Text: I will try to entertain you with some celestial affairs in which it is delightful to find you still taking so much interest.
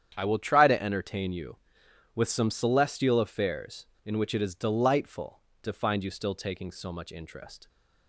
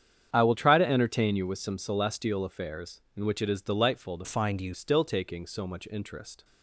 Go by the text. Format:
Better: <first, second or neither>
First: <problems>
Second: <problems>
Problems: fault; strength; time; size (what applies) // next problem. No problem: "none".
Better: first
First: starts louder than the rest; strong; until 1.1 s; 9 dB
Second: starts louder than the rest; strong; until 1.3 s; 8.5 dB // changes voice from "find" to "you"; from 4.2 to 4.7 s; 0.5 s long